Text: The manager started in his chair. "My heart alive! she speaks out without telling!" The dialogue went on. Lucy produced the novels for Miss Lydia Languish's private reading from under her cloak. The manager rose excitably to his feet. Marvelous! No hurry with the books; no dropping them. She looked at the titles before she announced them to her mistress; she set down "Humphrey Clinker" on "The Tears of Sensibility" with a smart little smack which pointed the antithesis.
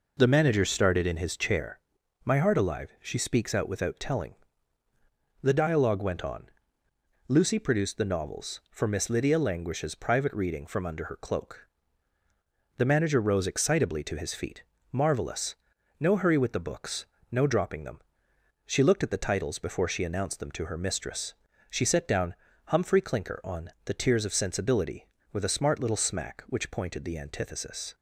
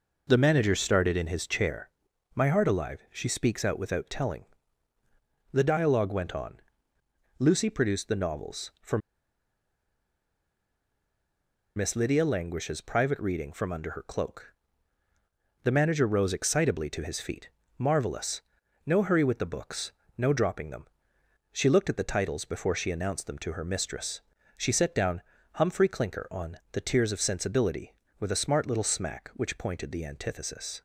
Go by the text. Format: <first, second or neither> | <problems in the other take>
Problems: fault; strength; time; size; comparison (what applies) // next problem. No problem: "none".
first | pauses between "for" and "Miss"; strong; at 8.9 s; 2.7 s long // pauses between "down" and "Humphrey"; slight; at 25.2 s; 0.34 s long; slight in the first